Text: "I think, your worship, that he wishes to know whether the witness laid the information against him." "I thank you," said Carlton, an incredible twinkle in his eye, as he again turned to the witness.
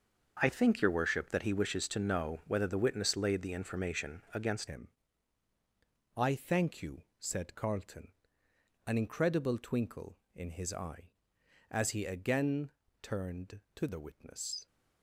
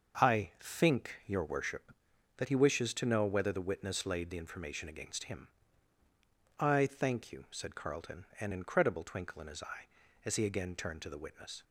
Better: second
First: starts louder than the rest; until 1.4 s; 6.5 dB // changes voice at "him"; from 4.6 s on; 10.0 s long // pauses between "again" and "turned"; slight; at 12.7 s; 0.32 s long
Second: starts louder than the rest; until 1.4 s; 6.5 dB

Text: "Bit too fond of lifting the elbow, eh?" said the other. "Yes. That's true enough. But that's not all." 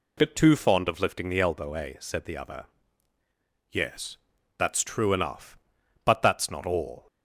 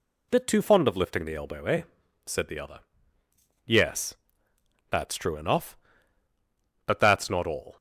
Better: neither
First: none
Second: none

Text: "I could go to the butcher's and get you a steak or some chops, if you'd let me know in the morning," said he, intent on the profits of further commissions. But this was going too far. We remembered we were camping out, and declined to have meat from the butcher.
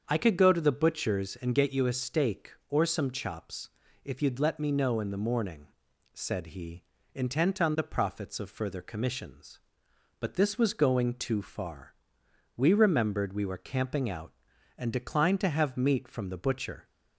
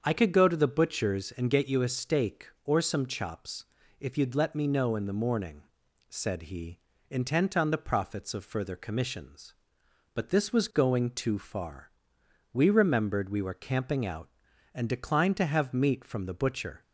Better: neither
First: starts louder than the rest; until 1.0 s; 7 dB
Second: starts louder than the rest; until 1.0 s; 7 dB

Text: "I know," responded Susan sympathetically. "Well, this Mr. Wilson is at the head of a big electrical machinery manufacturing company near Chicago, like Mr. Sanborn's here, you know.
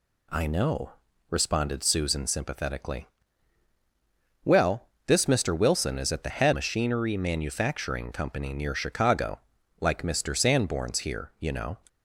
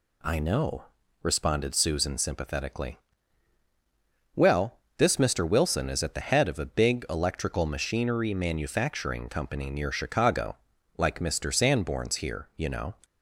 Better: second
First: skips "of a big electrical"; at 6.5 s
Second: none

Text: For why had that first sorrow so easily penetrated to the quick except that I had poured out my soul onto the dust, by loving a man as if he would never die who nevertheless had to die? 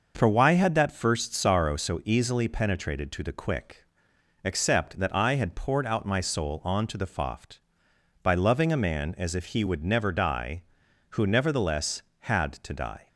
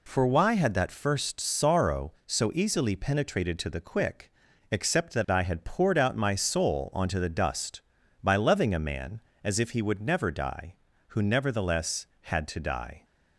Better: second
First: pauses between "quick" and "except"; noticeable; at 3.8 s; 0.60 s long // says "foft" for "dust"; at 7.0 s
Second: pauses between "quick" and "except"; at 4.3 s; 0.40 s long

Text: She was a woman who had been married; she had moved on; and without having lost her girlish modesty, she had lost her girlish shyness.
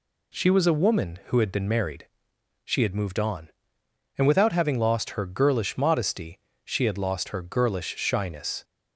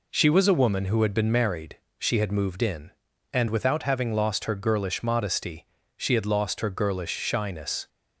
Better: first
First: none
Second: says "in" for "on"; at 2.6 s

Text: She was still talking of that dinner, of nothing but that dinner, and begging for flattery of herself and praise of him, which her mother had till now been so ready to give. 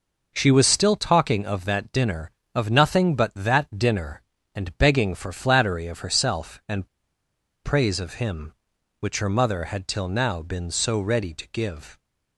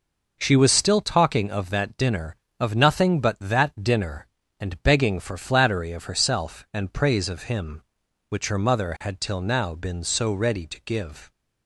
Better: second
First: pauses between "and" and "praise"; noticeable; at 6.8 s; 0.76 s long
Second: none

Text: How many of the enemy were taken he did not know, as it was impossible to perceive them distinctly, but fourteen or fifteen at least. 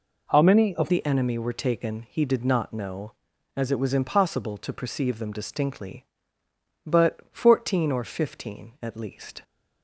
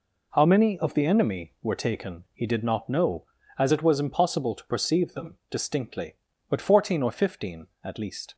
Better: second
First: changes voice at "the"; from 0.8 s on; 8.6 s long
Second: none

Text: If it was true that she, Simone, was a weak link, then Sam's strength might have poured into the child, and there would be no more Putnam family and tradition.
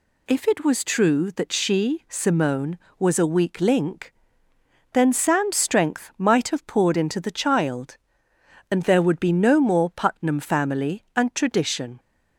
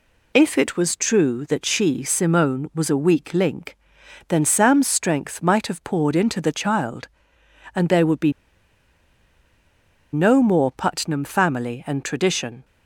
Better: first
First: none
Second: pauses between "be" and "no"; strong; at 8.3 s; 1.8 s long

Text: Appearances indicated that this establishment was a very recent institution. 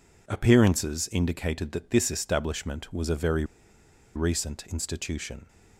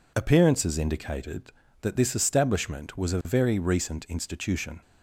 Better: second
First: pauses between "very" and "recent"; noticeable; at 3.4 s; 0.70 s long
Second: none

